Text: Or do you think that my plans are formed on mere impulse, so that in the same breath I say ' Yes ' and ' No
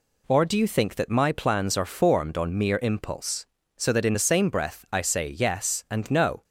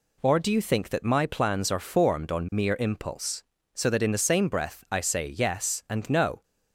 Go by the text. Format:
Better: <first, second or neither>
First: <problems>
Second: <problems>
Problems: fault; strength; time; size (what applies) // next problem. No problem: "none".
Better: neither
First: none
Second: none